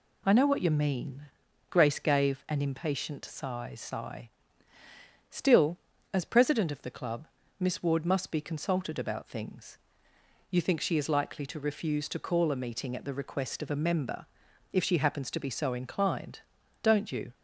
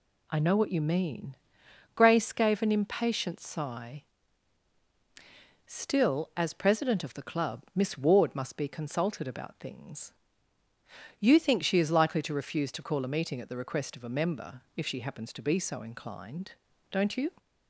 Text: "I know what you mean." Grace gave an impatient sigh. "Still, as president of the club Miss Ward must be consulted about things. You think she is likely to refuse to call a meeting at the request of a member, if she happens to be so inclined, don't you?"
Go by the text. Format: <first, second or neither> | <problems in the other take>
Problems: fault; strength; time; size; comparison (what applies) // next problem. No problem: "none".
second | says "sigh" twice; at 3.7 s // pauses between "club" and "Miss"; slight; at 7.2 s; 0.32 s long